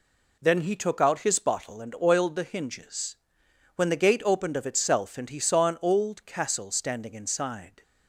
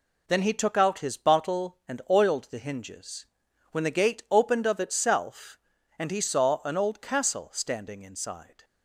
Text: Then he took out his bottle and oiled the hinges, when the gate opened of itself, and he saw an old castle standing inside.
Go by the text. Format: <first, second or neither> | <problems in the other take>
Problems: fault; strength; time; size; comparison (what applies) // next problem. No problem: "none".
neither | none